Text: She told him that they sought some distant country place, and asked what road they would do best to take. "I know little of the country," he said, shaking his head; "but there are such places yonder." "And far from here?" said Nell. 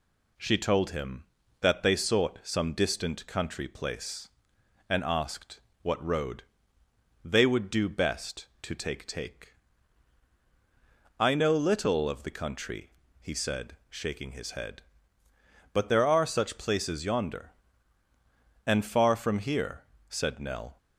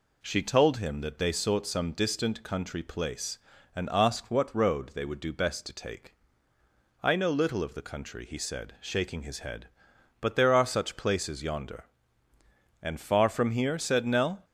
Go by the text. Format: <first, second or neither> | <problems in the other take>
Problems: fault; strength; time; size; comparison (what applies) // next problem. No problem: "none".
second | pauses between "asked" and "what"; slight; at 5.6 s; 0.20 s long // pauses between "road" and "they"; noticeable; at 6.4 s; 0.80 s long // says "take" twice; at 9.0 s